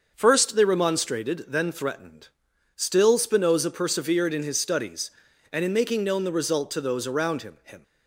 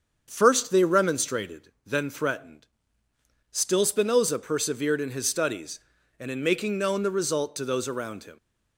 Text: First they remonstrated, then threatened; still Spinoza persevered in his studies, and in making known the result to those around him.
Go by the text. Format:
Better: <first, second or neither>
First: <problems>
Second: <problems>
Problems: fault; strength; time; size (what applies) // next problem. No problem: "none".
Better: second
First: starts louder than the rest; until 1.1 s; 6.5 dB // says "him" twice; at 7.6 s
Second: starts louder than the rest; until 1.2 s; 7 dB